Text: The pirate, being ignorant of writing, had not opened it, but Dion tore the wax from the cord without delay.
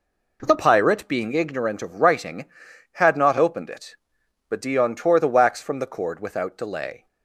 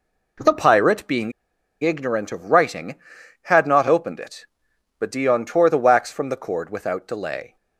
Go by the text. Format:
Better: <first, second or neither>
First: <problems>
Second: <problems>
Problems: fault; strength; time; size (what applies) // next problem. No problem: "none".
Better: first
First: none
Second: pauses between "being" and "ignorant"; noticeable; at 1.3 s; 0.50 s long